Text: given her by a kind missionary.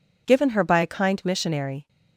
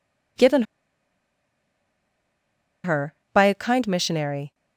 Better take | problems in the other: first | pauses between "given" and "her"; strong; at 0.6 s; 2.2 s long

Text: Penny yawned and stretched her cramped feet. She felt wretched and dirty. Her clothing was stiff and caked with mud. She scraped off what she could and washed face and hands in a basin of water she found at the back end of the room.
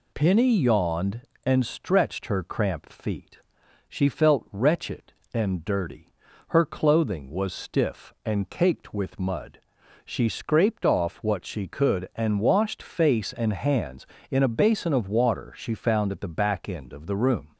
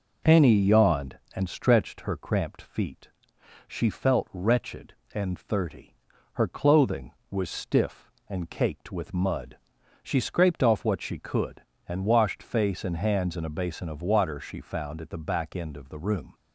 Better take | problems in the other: first | says "thirty" for "dirty"; at 5.3 s

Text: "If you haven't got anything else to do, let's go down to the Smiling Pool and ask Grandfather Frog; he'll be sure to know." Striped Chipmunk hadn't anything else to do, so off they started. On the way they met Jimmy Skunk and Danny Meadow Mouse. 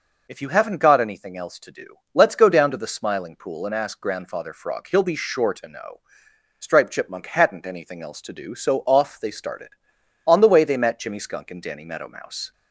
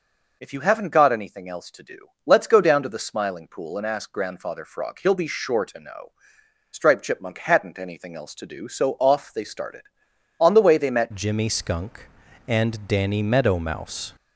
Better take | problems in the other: first | changes voice at "Jimmy"; from 11.1 s on; 3.0 s long

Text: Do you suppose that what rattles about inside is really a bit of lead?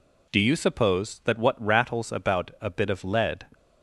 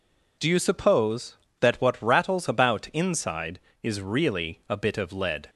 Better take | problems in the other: second | skips "inside is really"; at 2.5 s

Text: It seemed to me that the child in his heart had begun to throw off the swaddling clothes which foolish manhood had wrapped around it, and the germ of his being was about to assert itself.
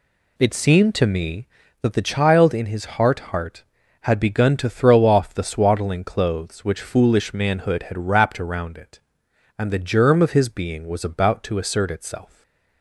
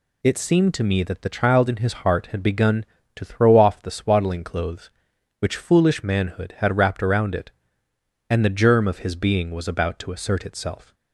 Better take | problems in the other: second | says "heart" twice; at 3.1 s // stays silent after the last word; slight; from 12.2 s on; 0.6 s long

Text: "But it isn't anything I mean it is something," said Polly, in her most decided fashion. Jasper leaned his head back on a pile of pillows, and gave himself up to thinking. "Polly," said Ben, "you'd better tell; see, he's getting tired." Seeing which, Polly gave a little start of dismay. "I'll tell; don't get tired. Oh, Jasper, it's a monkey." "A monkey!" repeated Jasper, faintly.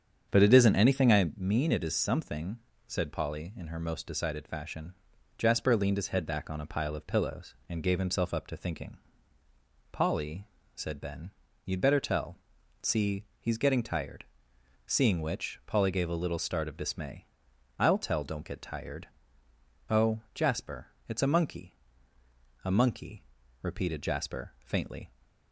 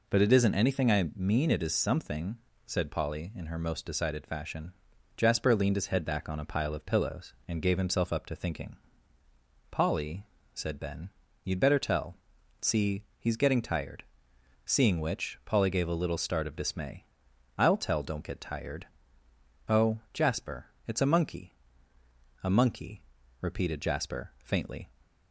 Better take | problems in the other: second | starts louder than the rest; strong; until 1.3 s; 7.5 dB

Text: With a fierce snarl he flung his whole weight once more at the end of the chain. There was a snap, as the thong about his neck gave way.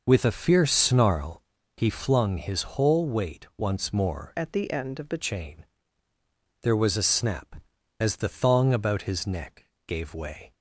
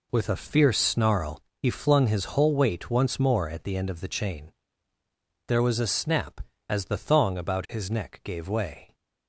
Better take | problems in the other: second | pauses between "snarl" and "he"; slight; at 1.4 s; 0.34 s long; slight in the second // changes voice from "at" to "the"; from 4.3 to 5.1 s; 0.8 s long // pauses between "neck" and "gave"; slight; at 9.6 s; 0.20 s long

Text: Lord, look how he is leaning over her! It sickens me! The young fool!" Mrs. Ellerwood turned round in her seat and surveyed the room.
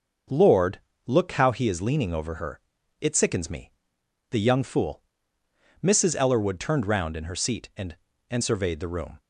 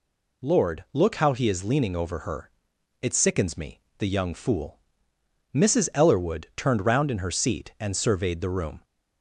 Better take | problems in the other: second | starts louder than the rest; until 1.5 s; 6 dB // says "and" twice; at 8.2 s

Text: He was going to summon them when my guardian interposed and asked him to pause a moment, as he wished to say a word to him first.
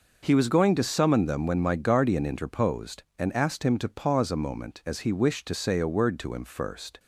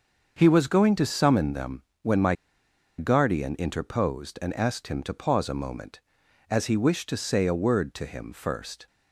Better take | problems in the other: first | starts louder than the rest; until 1.3 s; 6.5 dB // pauses between "them" and "when"; slight; at 1.8 s; 0.22 s long // pauses between "my" and "guardian"; noticeable; at 2.3 s; 0.63 s long

